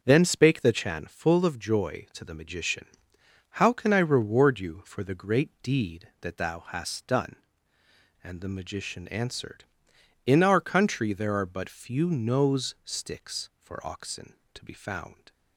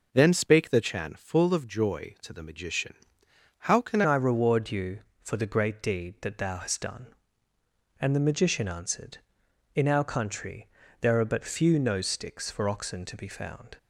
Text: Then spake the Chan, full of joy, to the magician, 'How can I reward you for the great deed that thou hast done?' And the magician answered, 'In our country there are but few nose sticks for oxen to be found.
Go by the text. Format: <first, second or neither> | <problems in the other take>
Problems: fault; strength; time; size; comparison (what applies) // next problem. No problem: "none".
first | changes voice at "I"; from 4.0 s on; 9.7 s long // pauses between "country" and "there"; slight; at 10.6 s; 0.32 s long